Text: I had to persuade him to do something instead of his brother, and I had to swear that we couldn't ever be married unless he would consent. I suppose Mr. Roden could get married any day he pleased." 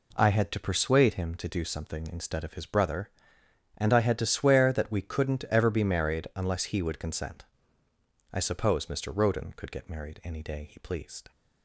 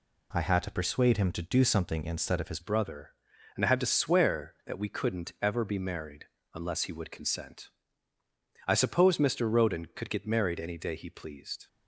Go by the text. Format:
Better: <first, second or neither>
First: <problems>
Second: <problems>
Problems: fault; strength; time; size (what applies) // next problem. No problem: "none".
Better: first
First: none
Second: changes voice at "brother"; from 2.6 s on; 9.0 s long // pauses between "married" and "unless"; slight; at 6.2 s; 0.28 s long